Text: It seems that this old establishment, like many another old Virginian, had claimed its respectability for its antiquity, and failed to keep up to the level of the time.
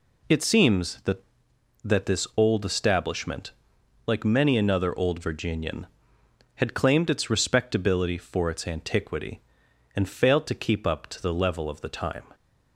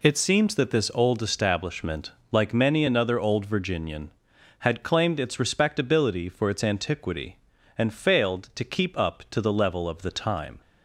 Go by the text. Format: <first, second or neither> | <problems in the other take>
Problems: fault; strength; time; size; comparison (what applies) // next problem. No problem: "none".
second | says "that" twice; at 1.8 s